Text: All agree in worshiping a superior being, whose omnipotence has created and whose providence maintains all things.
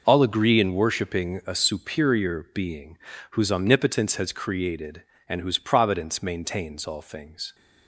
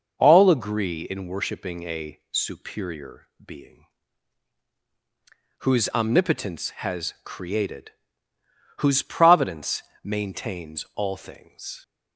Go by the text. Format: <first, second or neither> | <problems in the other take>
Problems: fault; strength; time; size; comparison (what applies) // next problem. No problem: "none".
first | pauses between "superior" and "being"; slight; at 3.2 s; 0.18 s long // skips "and"; at 8.3 s // pauses between "providence" and "maintains"; slight; at 9.8 s; 0.22 s long